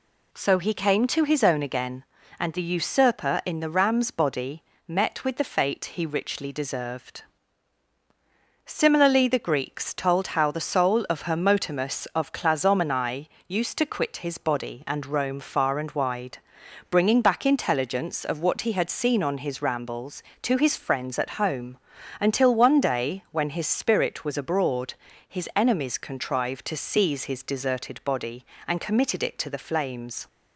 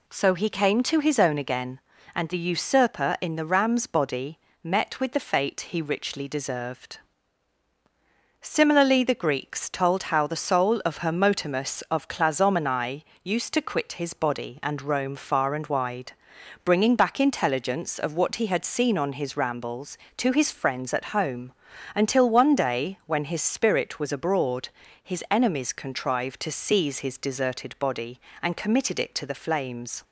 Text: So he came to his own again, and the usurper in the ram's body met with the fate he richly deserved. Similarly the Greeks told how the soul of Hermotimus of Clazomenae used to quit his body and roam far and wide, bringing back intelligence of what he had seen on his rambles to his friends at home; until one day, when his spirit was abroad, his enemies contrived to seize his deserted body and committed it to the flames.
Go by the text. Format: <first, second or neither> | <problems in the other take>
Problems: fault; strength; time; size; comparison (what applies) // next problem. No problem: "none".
neither | pauses between "body" and "met"; slight; the same in both // pauses between "Clazomenae" and "used"; slight; the same in both